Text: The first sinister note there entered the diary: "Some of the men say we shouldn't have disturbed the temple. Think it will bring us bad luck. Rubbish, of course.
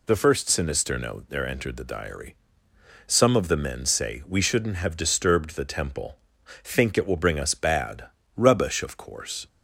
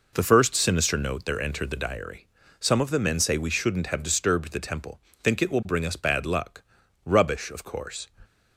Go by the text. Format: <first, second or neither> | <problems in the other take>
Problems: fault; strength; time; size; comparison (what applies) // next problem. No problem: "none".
second | skips "luck"; at 8.2 s